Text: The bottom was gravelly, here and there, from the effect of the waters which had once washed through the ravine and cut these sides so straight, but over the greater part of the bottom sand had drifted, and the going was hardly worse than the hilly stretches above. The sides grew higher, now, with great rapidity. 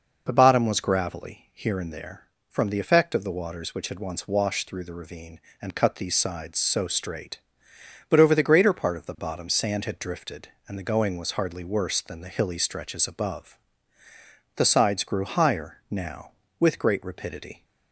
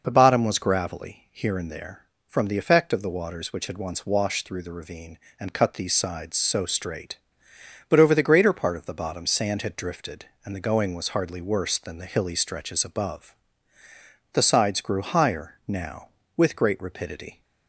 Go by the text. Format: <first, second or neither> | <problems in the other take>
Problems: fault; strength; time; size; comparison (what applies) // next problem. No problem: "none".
neither | none